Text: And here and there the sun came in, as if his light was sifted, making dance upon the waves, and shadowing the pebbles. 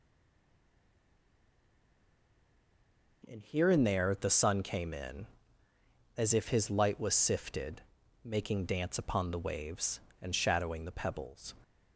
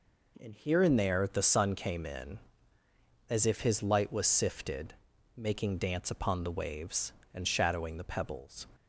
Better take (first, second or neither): second